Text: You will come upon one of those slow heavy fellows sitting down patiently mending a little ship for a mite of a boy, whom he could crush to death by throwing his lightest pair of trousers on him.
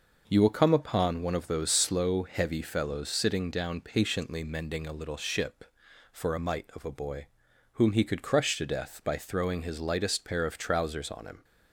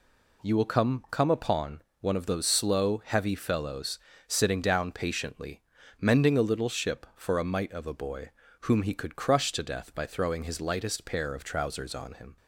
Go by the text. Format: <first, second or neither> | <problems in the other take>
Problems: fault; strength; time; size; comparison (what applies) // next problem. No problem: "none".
first | says "come" twice; at 1.0 s // pauses between "upon" and "one"; slight; at 1.8 s; 0.18 s long // pauses between "fellows" and "sitting"; slight; at 3.9 s; 0.28 s long // pauses between "patiently" and "mending"; at 5.6 s; 0.39 s long